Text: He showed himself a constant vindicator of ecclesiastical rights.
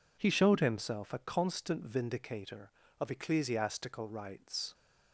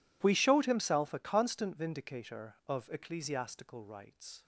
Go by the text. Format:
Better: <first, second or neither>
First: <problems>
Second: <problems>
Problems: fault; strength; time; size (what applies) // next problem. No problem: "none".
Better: first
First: none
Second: says "We" for "He"; at 0.2 s